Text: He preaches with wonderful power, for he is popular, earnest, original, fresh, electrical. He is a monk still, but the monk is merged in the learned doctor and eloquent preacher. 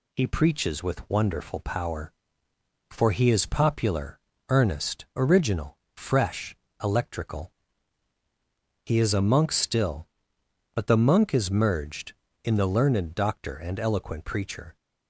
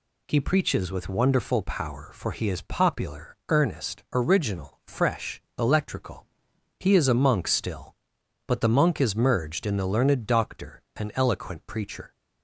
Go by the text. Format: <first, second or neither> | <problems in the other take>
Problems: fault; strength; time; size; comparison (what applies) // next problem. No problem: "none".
neither | none